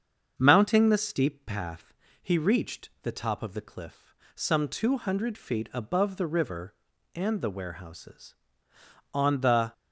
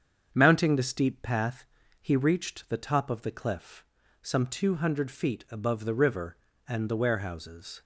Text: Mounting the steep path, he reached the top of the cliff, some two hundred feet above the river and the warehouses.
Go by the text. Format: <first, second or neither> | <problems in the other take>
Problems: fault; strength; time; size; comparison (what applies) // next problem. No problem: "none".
second | starts louder than the rest; until 1.3 s; 7 dB; strong in the second // goes on to say "On the"; from 9.1 s on; 0.58 s long